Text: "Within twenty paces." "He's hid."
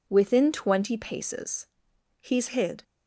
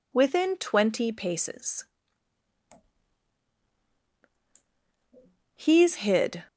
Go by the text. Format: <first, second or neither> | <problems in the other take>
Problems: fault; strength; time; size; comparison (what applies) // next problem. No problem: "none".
neither | none